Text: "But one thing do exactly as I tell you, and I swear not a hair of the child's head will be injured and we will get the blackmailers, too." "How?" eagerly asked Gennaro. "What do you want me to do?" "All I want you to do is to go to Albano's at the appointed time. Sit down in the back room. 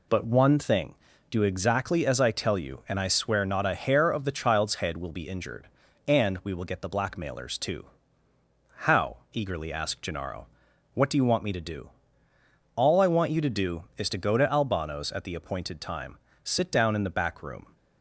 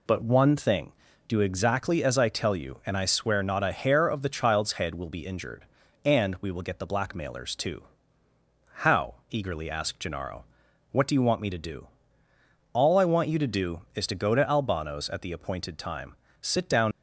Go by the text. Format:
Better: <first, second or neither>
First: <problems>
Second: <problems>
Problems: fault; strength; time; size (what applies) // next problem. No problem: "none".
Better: first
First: none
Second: stops before "in the back room"; at 16.9 s